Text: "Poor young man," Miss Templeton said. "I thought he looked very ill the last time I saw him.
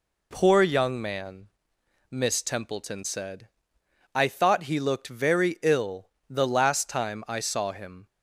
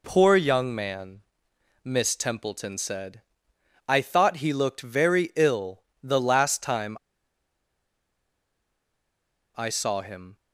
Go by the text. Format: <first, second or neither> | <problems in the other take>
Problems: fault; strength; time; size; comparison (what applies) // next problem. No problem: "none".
first | pauses between "ill" and "the"; slight; at 5.8 s; 0.22 s long; slight in the first // pauses between "time" and "I"; strong; at 6.9 s; 2.6 s long